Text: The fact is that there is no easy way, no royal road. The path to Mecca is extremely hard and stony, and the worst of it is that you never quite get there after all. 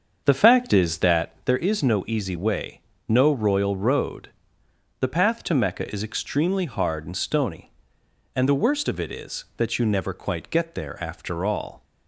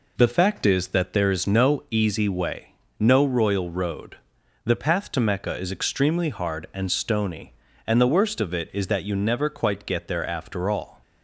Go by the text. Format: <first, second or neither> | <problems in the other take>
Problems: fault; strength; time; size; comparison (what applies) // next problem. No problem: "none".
second | starts louder than the rest; until 1.4 s; 7 dB